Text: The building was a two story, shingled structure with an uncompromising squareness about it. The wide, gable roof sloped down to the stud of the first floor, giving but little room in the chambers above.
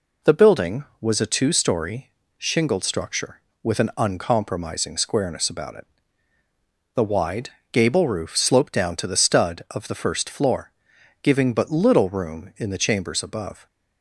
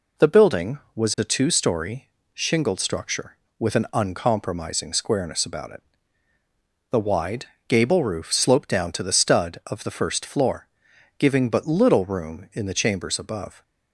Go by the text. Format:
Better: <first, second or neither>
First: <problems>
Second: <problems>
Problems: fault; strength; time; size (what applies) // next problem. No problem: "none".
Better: neither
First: none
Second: none